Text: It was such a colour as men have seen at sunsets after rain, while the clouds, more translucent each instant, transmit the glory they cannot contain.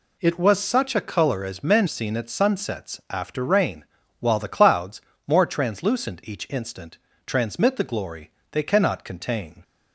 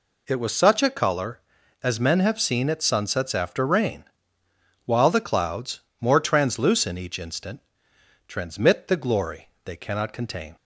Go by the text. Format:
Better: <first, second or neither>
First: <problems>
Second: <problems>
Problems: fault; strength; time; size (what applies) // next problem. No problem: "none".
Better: second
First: skips "have"; at 1.8 s // pauses between "glory" and "they"; slight; at 8.3 s; 0.20 s long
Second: pauses between "glory" and "they"; slight; at 9.4 s; 0.16 s long